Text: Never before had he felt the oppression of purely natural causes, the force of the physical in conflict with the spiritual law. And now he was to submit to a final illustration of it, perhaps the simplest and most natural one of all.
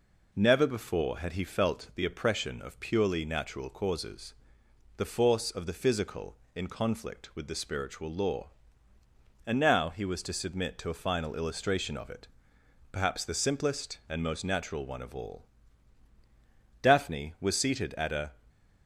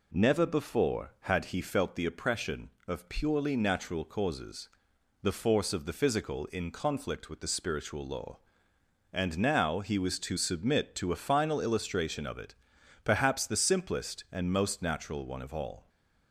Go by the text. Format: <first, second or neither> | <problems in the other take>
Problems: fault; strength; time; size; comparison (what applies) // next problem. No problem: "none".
second | goes on to say "Daphne was seated at a"; from 16.8 s on; 1.5 s long